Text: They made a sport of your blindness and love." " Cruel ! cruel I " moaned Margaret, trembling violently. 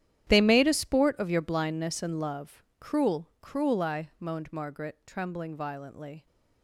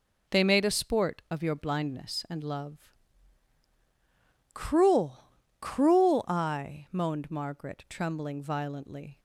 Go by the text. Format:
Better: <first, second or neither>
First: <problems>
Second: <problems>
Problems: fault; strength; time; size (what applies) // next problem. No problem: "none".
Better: second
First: gets quieter; strong; throughout; 16 dB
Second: none